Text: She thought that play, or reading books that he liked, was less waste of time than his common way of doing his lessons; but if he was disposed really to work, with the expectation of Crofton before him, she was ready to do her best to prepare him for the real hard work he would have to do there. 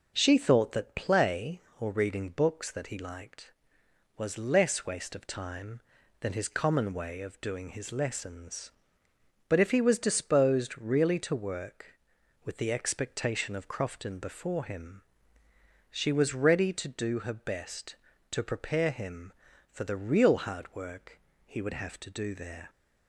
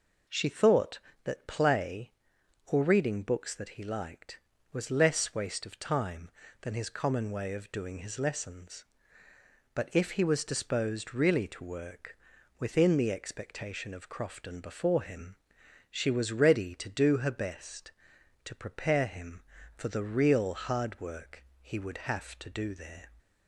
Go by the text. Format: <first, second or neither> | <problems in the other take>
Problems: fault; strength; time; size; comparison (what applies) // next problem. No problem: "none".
first | says "within" for "with"; at 12.5 s // pauses between "work" and "he"; slight; at 21.4 s; 0.16 s long; slight in the first